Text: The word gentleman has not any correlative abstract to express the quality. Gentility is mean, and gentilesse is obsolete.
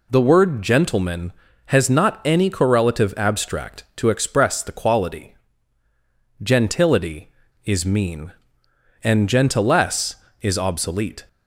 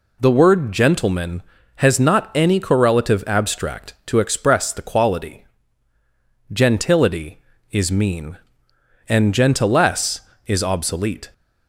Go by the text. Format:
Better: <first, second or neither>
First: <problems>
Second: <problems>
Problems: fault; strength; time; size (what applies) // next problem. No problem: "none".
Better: neither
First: none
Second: none